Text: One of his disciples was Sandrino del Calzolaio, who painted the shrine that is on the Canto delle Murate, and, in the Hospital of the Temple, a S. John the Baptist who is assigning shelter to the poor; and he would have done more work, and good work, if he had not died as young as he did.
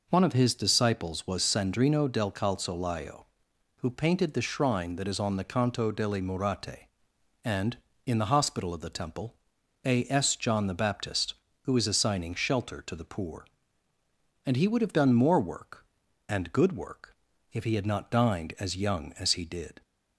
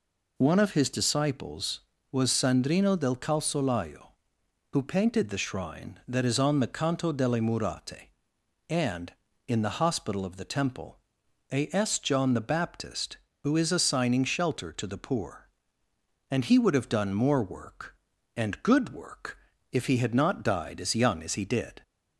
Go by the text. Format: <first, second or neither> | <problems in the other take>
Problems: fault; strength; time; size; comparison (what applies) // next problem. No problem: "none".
second | says "dined" for "died"; at 18.1 s